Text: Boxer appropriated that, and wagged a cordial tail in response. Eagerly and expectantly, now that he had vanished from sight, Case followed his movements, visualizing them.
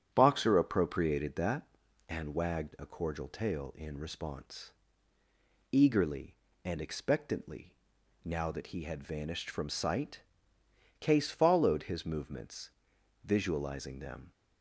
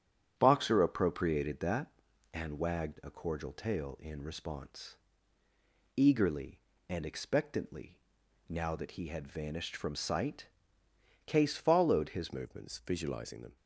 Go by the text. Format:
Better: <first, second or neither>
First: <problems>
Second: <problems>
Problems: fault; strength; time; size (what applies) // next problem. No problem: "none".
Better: first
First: starts louder than the rest; strong; until 1.1 s; 8.5 dB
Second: starts louder than the rest; strong; until 1.3 s; 9 dB // changes voice at "movements"; from 12.3 s on; 1.2 s long